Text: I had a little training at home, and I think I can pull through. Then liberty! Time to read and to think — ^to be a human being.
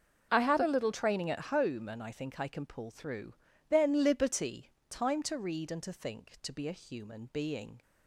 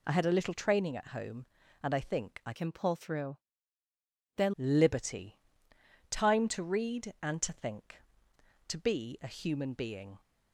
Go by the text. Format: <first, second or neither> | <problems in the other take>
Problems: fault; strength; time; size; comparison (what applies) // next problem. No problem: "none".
first | changes voice from "can" to "Then"; from 2.5 to 4.5 s; 2.0 s long